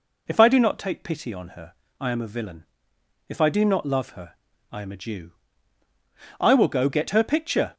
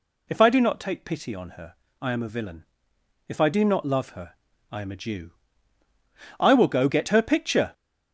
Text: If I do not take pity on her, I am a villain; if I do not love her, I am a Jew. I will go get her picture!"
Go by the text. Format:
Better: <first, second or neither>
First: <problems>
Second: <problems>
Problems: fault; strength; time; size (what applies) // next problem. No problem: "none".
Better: first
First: none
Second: gets louder; noticeable; throughout; 6 dB